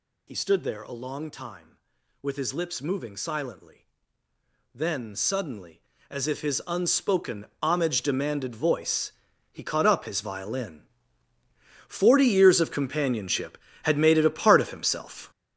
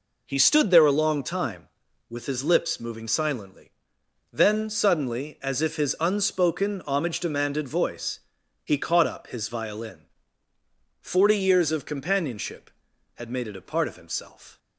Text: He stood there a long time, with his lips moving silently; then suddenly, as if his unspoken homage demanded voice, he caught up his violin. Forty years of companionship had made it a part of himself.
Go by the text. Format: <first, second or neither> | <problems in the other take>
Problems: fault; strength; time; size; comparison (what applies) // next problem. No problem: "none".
second | gets louder; strong; throughout; 10 dB // pauses between "unspoken" and "homage"; slight; at 7.4 s; 0.16 s long